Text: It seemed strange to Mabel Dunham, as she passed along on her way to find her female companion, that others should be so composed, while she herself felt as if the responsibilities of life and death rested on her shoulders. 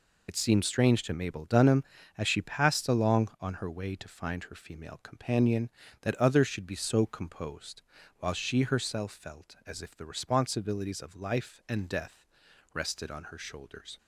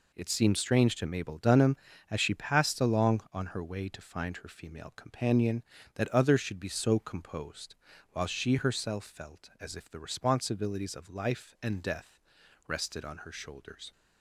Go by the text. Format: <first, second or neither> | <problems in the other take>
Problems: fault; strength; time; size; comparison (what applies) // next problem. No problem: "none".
second | loses the start of "It"; at 0.2 s; 70 ms // pauses between "death" and "rested"; noticeable; at 12.2 s; 0.48 s long; noticeable in the second